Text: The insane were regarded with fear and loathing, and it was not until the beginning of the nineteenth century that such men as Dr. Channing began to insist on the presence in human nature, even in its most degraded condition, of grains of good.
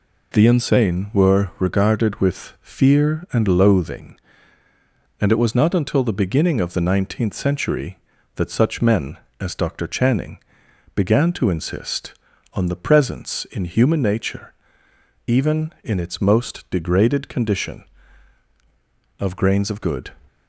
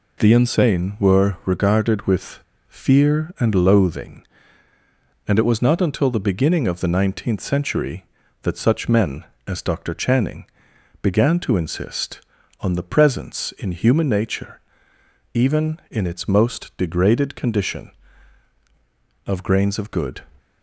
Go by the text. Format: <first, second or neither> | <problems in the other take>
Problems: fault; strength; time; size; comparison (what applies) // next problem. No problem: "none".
first | pauses between "with" and "fear"; slight; at 2.4 s; 0.28 s long // pauses between "Channing" and "began"; noticeable; at 10.4 s; 0.56 s long; noticeable in the first